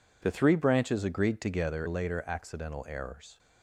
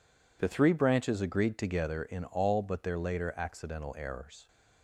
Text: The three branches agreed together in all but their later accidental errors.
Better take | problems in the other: second | skips "in all but their"; at 1.8 s

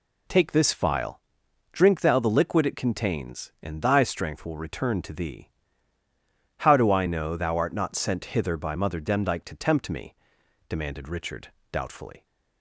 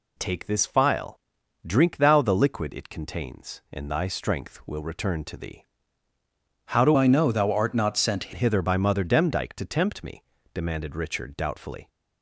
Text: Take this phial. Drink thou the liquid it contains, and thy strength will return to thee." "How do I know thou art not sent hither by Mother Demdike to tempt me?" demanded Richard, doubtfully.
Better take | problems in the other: first | changes voice from "I" to "sent"; from 6.9 to 8.3 s; 1.4 s long

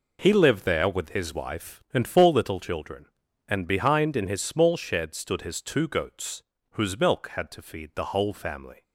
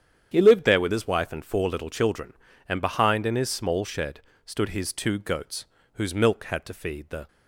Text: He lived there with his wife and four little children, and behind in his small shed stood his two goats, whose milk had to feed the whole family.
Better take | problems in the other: first | starts louder than the rest; strong; until 1.3 s; 9 dB // pauses between "shed" and "stood"; slight; at 4.2 s; 0.24 s long // stops before "whole family"; at 7.2 s

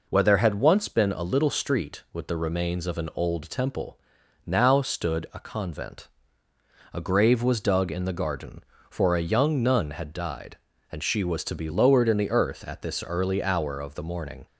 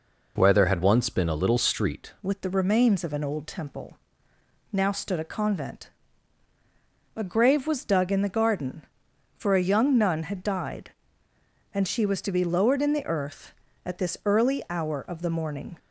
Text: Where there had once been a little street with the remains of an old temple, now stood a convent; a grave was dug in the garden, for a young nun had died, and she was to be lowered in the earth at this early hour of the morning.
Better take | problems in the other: first | changes voice at "with"; from 2.2 s on; 13.5 s long

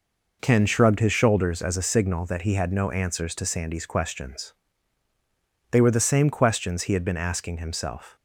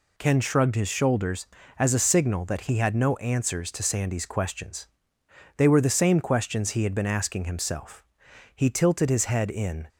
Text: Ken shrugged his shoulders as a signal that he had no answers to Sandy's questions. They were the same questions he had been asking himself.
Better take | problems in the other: first | goes on to say "He tilted his head in"; from 8.5 s on; 1.3 s long

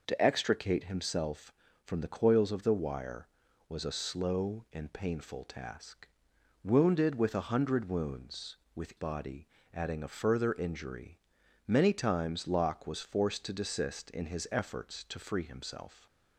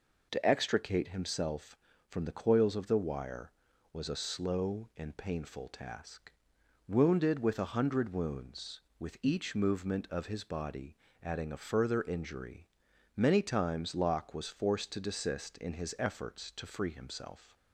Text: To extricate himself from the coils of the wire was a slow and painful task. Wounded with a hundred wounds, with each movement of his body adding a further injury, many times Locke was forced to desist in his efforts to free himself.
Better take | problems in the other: second | skips "each movement of his"; at 8.9 s // pauses between "body" and "adding"; slight; at 9.4 s; 0.26 s long; slight in the second

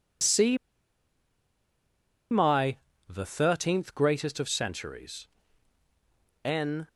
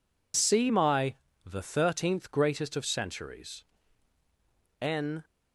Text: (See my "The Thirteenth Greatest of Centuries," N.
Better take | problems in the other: second | pauses between "See" and "my"; strong; at 0.5 s; 1.7 s long // pauses between "my" and "The"; slight; at 2.7 s; 0.32 s long; slight in the second

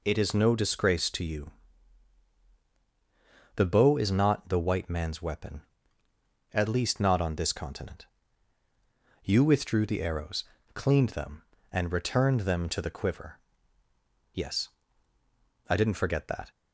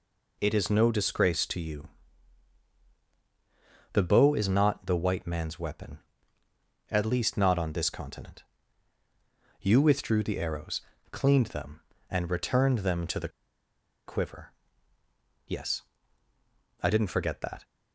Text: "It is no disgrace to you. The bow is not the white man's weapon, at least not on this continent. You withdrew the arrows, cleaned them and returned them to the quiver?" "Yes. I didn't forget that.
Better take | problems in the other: first | pauses between "the" and "quiver"; noticeable; at 13.2 s; 0.77 s long

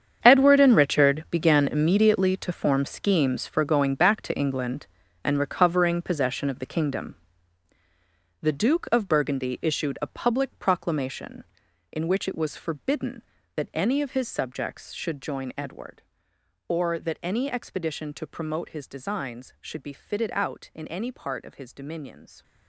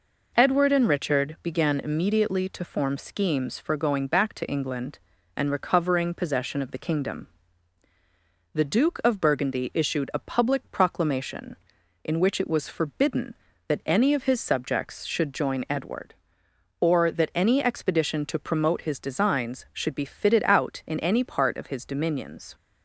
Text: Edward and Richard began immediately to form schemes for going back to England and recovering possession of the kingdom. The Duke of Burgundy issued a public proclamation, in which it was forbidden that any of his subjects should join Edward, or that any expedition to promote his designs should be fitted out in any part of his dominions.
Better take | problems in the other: second | gets quieter; strong; throughout; 15 dB

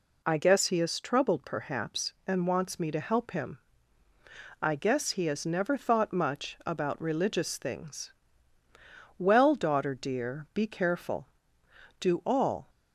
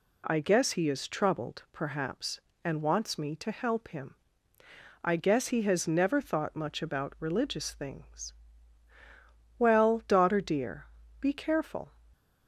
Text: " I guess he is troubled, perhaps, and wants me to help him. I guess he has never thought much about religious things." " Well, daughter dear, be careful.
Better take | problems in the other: second | goes on to say "Do all"; noticeable; from 11.9 s on; 0.70 s long

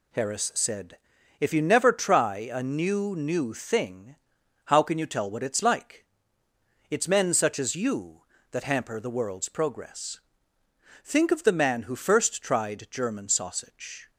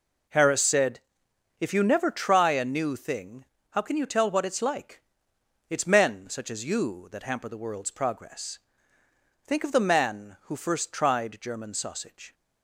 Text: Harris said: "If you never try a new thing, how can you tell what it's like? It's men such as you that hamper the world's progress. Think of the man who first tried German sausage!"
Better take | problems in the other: second | says "new" twice; at 3.1 s

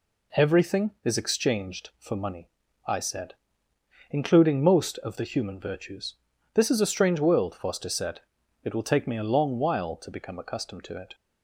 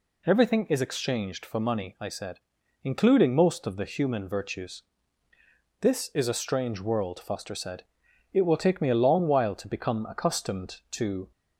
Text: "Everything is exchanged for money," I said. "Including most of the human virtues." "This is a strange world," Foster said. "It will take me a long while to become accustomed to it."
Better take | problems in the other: first | stops before "it"; at 11.3 s

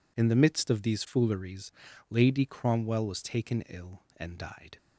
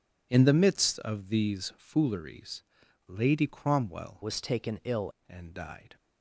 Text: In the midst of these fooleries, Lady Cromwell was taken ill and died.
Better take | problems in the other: first | changes voice from "was" to "ill"; from 4.2 to 5.1 s; 0.9 s long

